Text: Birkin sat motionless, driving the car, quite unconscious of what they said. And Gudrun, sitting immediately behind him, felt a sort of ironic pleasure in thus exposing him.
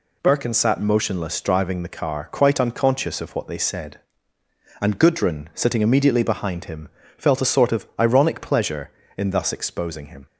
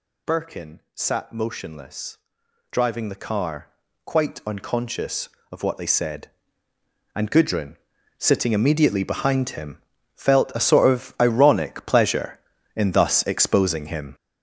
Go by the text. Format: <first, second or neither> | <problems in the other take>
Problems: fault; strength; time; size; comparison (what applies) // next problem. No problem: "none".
first | gets louder; strong; throughout; 8.5 dB